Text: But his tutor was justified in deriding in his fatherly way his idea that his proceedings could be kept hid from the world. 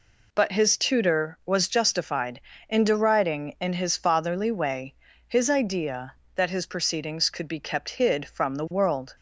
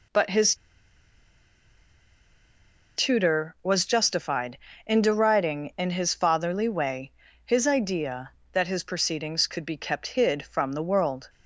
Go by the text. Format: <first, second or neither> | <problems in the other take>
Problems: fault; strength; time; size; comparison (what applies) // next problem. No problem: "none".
first | pauses between "his" and "tutor"; strong; at 0.5 s; 2.4 s long // pauses between "way" and "his"; slight; at 7.1 s; 0.32 s long; slight in the first